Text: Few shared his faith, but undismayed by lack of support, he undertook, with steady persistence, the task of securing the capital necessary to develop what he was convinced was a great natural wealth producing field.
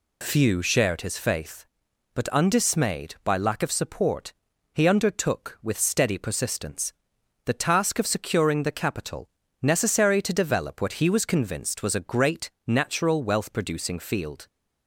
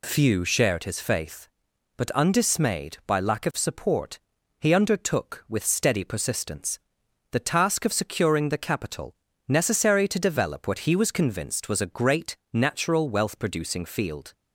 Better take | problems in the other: neither | pauses between "capital" and "necessary"; slight; the same in both // pauses between "great" and "natural"; slight; the same in both

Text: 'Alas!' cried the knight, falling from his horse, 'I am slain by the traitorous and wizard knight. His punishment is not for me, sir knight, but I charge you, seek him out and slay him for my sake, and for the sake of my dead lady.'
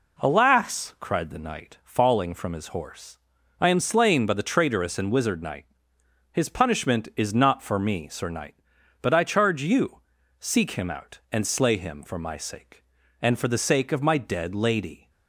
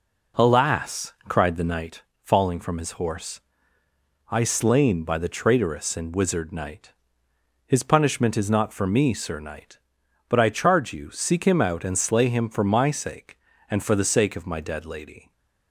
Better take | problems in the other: first | skips "am"; at 4.4 s // stays silent after the last word; slight; from 15.1 s on; 0.6 s long

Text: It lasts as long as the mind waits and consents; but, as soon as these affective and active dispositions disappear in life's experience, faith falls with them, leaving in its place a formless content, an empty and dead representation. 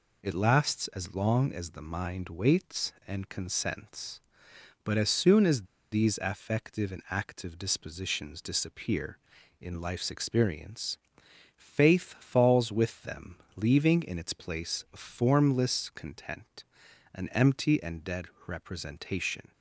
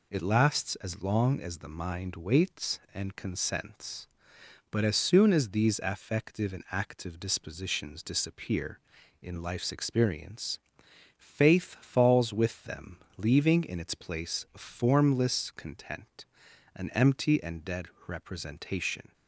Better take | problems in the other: second | pauses between "as" and "these"; slight; at 5.6 s; 0.26 s long // pauses between "dead" and "representation"; slight; at 18.2 s; 0.20 s long; slight in the second

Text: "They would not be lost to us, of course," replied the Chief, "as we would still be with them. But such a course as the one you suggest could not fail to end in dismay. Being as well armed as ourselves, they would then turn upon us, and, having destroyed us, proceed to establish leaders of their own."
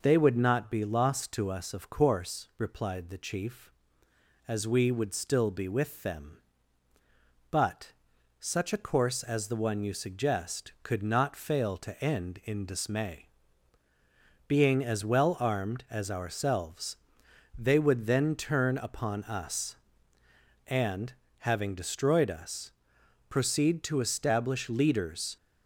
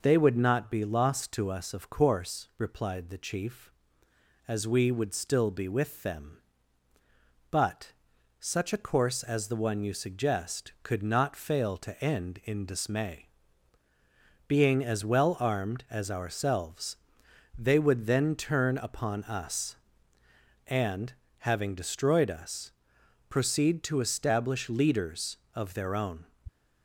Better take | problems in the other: second | pauses between "But" and "such"; noticeable; at 7.9 s; 0.46 s long; noticeable in the second // stops before "of their own"; at 25.3 s

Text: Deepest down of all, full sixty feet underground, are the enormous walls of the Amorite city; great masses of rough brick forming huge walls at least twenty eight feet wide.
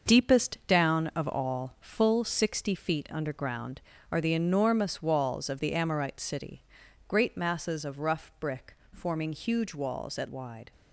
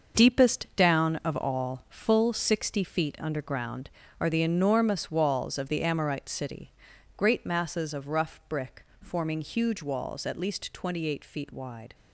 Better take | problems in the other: second | starts louder than the rest; until 1.2 s; 6.5 dB; also in the second // pauses between "brick" and "forming"; slight; at 8.7 s; 0.16 s long; slight in the second // skips "least twenty eight feet"; at 10.2 s

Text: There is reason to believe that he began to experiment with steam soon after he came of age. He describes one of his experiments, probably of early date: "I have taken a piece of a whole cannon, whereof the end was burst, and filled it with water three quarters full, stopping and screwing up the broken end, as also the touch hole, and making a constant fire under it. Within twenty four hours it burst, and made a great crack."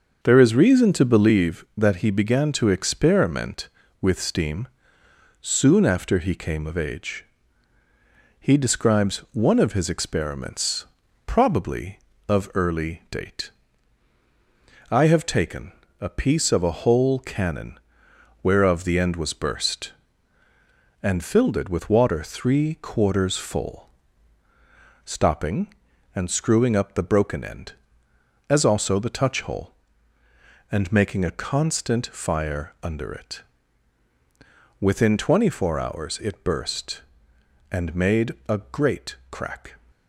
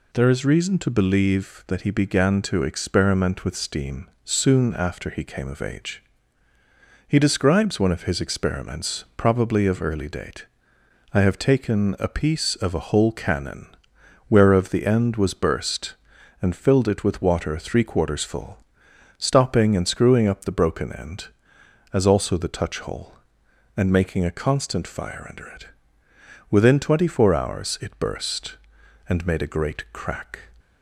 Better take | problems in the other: second | starts louder than the rest; until 1.5 s; 6 dB // pauses between "steam" and "soon"; noticeable; at 4.6 s; 0.74 s long; slight in the second // pauses between "taken" and "a"; slight; at 15.7 s; 0.28 s long

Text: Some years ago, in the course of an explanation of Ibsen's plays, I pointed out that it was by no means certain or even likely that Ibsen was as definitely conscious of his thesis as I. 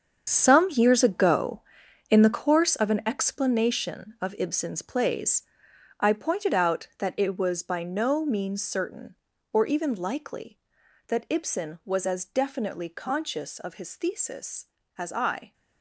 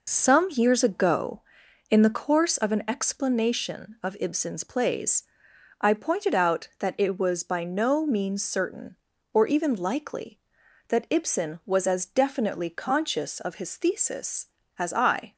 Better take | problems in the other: second | gets quieter; strong; throughout; 12.5 dB

